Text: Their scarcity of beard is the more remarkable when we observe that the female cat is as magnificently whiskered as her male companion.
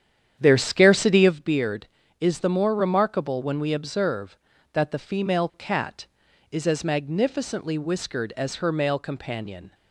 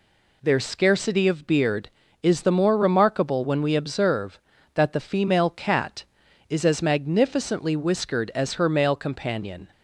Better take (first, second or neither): second